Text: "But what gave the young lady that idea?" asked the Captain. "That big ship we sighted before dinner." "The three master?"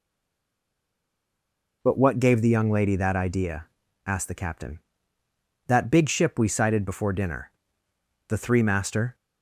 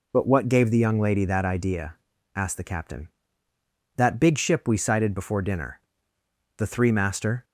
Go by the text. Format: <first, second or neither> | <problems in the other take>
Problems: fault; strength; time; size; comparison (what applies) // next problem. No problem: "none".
second | stays silent before the first word; noticeable; until 1.8 s; 1.8 s long